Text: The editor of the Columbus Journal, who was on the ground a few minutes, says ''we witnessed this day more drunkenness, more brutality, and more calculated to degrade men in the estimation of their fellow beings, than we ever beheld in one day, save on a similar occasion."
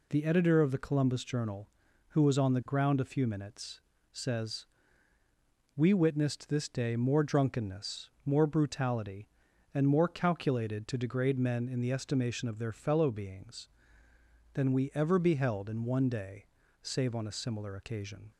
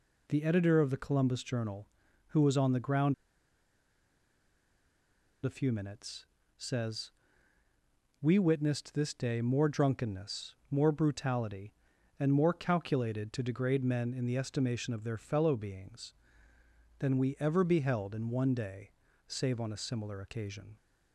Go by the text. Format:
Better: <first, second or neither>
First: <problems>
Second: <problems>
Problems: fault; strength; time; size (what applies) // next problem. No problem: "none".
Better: first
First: pauses between "says" and "we"; at 4.6 s; 1.1 s long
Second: pauses between "ground" and "a"; strong; at 3.1 s; 2.2 s long // pauses between "says" and "we"; at 7.0 s; 1.1 s long